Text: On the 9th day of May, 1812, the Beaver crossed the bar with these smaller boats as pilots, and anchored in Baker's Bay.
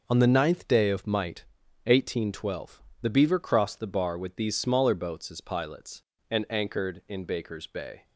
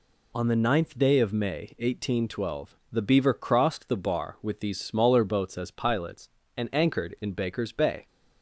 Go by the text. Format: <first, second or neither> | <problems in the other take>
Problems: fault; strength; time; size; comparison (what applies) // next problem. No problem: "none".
second | says "Might" for "May"; at 1.0 s